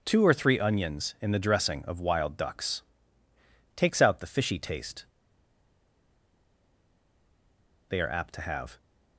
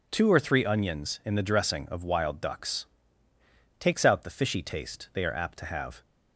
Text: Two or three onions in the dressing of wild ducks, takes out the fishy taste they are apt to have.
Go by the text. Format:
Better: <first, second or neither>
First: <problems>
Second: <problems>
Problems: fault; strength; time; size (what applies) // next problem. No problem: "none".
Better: second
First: pauses between "taste" and "they"; strong; at 5.0 s; 2.8 s long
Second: none